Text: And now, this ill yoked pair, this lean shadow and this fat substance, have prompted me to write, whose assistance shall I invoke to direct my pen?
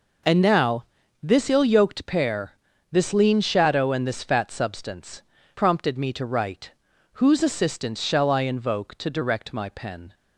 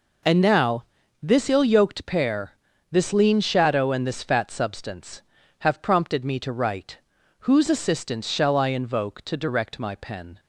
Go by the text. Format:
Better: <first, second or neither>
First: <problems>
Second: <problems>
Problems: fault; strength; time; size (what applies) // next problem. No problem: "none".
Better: second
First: skips "have"; at 5.3 s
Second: none